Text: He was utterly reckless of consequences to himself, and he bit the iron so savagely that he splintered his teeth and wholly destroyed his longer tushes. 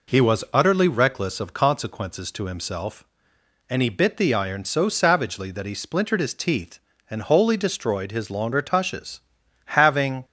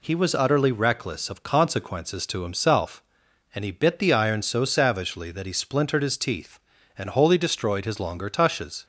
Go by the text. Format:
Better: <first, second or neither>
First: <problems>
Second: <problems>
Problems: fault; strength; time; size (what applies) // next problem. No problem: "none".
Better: second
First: goes on to say "Having"; slight; from 9.7 s on; 0.48 s long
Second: none